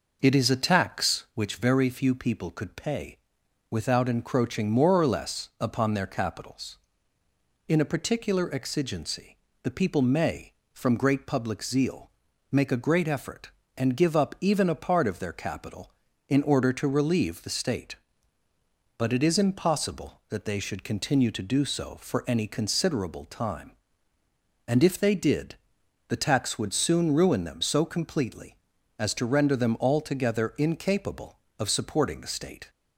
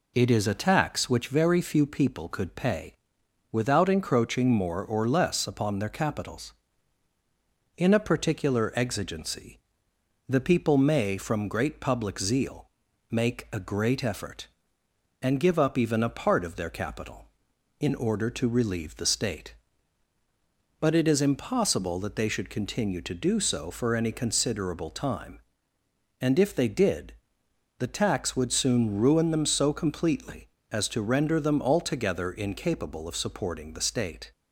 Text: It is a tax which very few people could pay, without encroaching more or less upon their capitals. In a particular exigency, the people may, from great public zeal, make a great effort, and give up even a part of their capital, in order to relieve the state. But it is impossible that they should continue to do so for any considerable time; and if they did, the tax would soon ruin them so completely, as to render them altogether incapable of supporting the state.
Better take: second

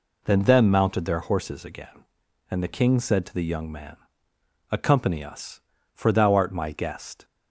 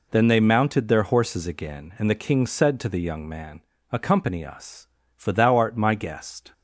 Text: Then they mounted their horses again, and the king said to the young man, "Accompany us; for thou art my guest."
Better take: second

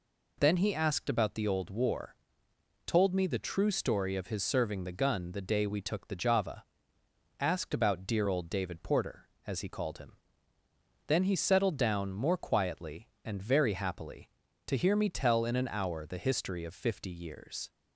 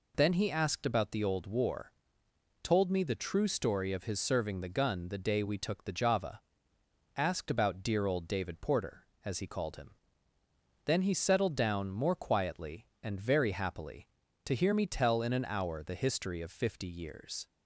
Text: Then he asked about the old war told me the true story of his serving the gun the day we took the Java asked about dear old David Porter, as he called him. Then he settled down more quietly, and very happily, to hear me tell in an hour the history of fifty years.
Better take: neither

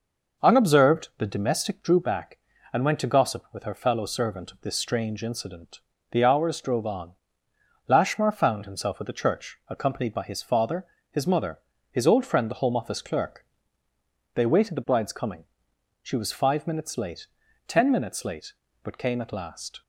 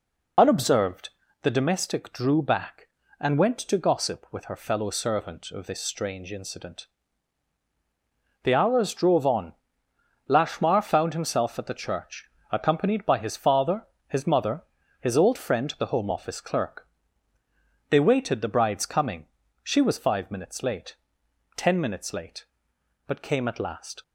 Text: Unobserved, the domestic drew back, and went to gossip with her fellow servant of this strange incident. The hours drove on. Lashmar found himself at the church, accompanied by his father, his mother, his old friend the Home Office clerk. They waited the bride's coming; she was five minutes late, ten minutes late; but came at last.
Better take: first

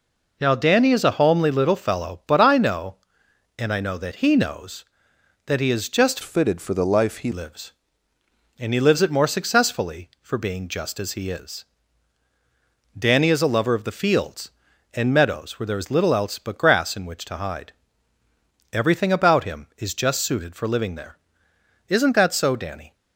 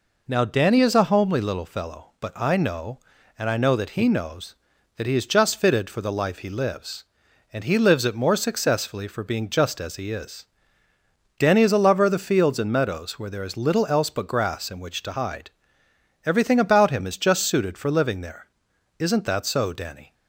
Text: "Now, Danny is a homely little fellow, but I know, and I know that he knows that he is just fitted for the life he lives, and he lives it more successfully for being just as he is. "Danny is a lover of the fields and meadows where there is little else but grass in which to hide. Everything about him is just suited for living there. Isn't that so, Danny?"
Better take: second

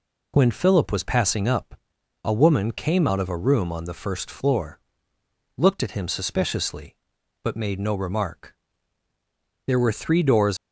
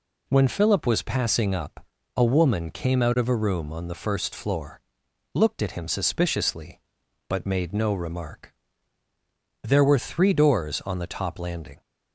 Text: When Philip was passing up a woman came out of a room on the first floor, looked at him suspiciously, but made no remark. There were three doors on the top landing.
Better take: second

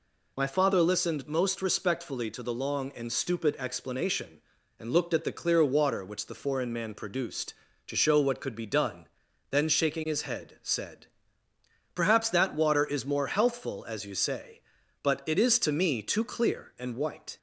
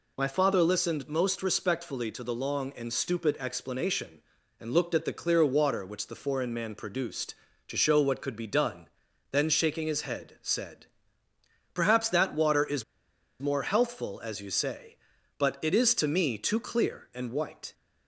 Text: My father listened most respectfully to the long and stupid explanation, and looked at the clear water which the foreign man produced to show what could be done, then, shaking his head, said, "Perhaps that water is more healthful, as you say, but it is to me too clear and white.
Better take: first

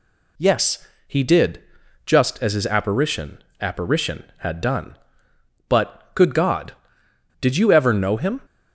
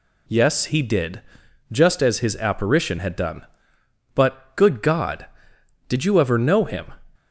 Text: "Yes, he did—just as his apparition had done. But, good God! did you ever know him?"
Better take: second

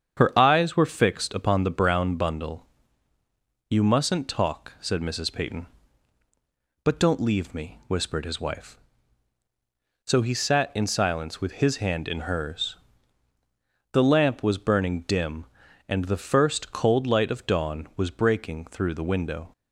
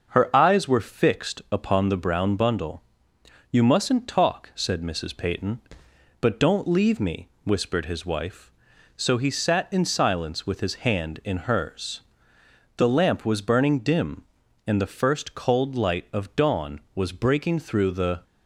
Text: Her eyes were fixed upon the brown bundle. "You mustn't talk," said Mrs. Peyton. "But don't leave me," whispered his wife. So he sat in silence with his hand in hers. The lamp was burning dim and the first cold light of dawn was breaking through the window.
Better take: first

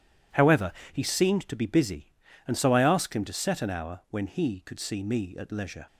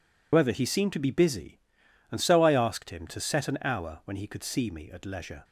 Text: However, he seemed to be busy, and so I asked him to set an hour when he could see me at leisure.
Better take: first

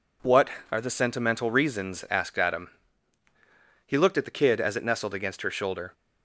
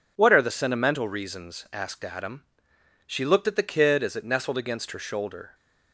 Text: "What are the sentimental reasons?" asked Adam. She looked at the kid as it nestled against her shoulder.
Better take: second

